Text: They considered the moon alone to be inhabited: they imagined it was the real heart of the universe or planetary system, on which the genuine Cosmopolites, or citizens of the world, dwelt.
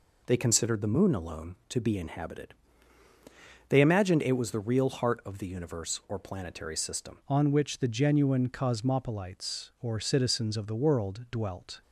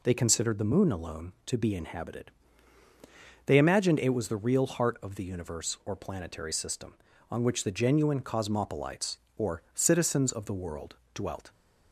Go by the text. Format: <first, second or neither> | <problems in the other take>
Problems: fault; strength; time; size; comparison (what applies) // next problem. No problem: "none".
second | changes voice at "on"; from 7.2 s on; 4.6 s long